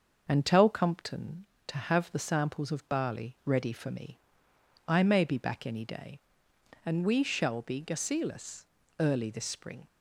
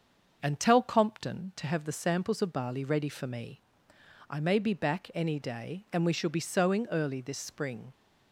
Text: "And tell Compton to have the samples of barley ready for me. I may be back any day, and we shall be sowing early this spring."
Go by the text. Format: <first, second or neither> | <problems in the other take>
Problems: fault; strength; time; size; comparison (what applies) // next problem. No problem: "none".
second | starts louder than the rest; until 1.2 s; 6.5 dB; also in the second // says "gasilus" for "sowing"; at 7.8 s